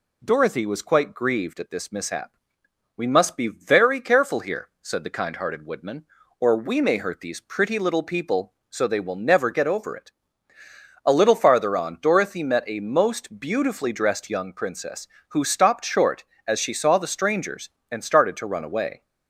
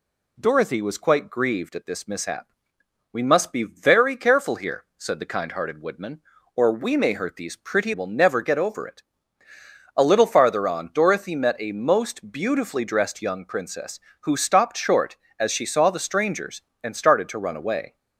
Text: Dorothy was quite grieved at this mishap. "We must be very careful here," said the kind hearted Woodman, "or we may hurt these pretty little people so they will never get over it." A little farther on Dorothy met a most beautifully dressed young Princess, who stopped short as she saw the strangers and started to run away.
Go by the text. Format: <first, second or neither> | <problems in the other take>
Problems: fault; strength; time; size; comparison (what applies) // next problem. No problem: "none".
first | skips "little people so they"; at 7.9 s